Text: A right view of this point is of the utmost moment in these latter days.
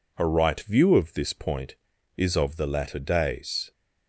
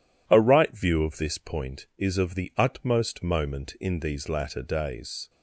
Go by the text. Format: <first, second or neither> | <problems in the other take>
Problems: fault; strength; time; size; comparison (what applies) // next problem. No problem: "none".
second | skips "utmost moment in these"; at 2.6 s